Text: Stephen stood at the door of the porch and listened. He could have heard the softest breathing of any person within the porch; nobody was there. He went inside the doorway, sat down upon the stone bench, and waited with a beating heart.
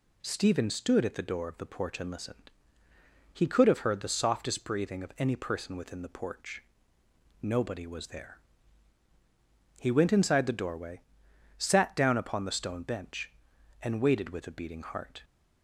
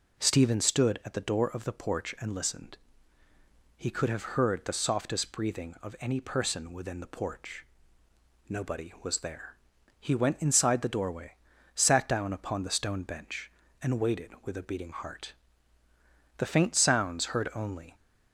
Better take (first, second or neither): first